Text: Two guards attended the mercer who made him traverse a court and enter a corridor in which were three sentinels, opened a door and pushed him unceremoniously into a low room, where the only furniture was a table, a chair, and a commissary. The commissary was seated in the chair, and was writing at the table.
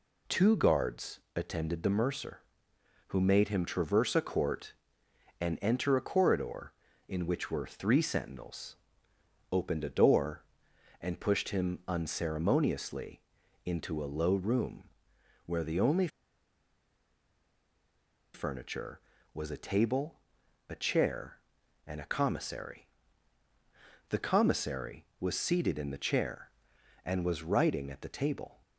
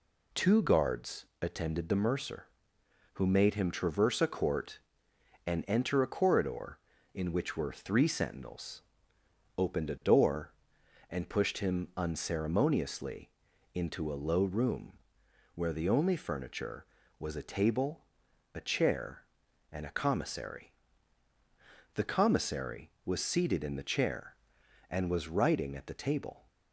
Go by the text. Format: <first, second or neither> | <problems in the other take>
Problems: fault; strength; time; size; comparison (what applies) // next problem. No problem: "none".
second | pauses between "guards" and "attended"; slight; at 1.1 s; 0.16 s long; slight in the second // pauses between "unceremoniously" and "into"; noticeable; at 13.1 s; 0.46 s long; noticeable in the second // pauses between "only" and "furniture"; strong; at 16.0 s; 2.2 s long